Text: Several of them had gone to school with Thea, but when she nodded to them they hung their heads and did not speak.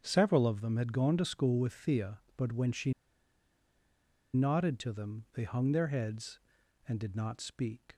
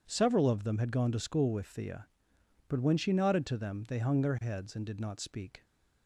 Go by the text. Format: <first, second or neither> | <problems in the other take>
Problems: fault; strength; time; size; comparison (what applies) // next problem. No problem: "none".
second | starts louder than the rest; strong; until 1.0 s; 8 dB // pauses between "she" and "nodded"; strong; at 2.9 s; 1.4 s long